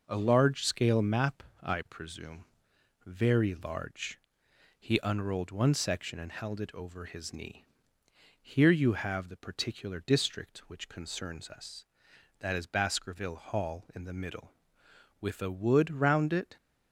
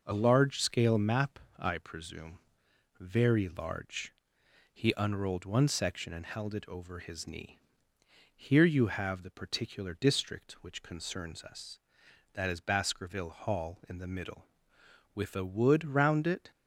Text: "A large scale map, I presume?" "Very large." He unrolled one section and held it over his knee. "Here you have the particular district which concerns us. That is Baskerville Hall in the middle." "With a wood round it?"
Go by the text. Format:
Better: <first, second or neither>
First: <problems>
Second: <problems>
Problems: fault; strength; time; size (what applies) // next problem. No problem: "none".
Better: neither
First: none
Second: none